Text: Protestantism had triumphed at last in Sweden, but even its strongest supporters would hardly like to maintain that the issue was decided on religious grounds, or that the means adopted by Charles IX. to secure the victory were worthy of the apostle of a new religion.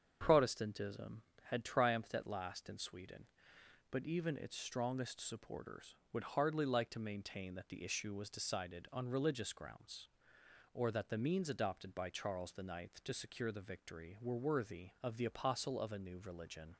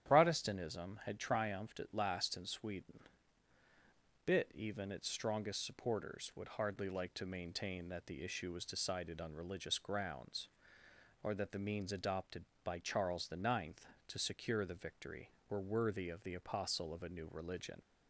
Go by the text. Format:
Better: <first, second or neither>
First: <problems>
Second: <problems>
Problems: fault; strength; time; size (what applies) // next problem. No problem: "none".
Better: first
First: starts louder than the rest; strong; until 1.2 s; 7.5 dB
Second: starts louder than the rest; strong; until 1.1 s; 10 dB // says "bit" for "but"; at 4.2 s